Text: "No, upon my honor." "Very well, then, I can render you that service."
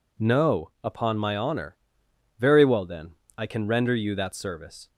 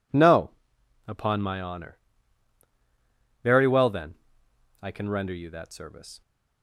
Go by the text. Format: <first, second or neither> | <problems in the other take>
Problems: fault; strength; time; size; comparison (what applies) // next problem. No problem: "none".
neither | none